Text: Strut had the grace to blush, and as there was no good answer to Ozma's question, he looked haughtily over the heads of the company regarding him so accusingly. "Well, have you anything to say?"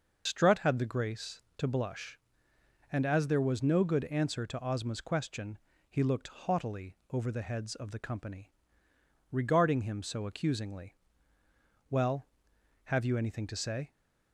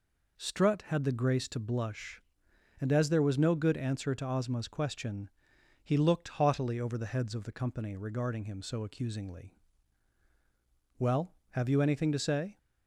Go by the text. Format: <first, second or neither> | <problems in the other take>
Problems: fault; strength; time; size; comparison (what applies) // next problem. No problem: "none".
second | loses the start of "Strut"; at 0.2 s; 60 ms // pauses between "haughtily" and "over"; slight; at 6.9 s; 0.16 s long // pauses between "company" and "regarding"; noticeable; at 8.5 s; 0.80 s long